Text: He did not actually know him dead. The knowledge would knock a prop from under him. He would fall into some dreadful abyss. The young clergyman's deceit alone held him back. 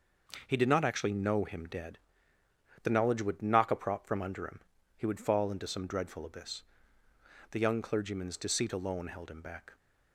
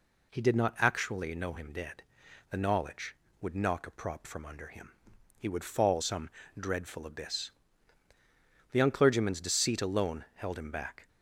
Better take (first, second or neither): first